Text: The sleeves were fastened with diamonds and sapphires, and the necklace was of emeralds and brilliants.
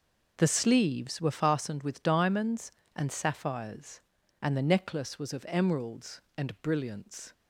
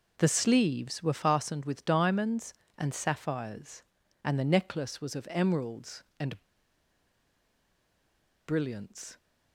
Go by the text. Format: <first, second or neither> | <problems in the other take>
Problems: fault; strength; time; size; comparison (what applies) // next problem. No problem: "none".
first | pauses between "and" and "brilliants"; strong; at 6.4 s; 2.0 s long